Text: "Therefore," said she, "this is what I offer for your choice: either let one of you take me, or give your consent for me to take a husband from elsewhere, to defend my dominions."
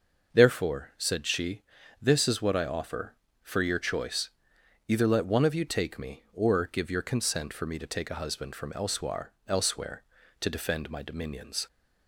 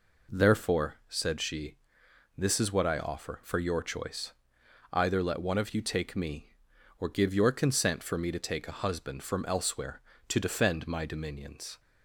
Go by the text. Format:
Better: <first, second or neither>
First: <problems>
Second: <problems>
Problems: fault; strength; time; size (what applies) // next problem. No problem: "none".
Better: second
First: starts louder than the rest; noticeable; until 1.3 s; 6 dB // says "elsewhere" twice; at 9.4 s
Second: none